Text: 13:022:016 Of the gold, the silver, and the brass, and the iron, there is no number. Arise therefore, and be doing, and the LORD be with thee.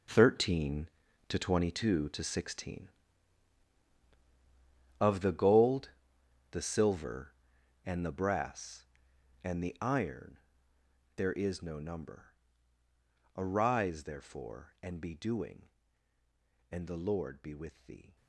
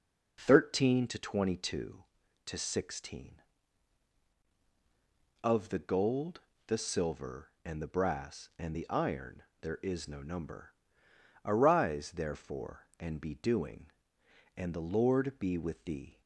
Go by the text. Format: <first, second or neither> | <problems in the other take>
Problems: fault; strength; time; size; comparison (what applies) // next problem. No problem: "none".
second | gets quieter; strong; throughout; 12 dB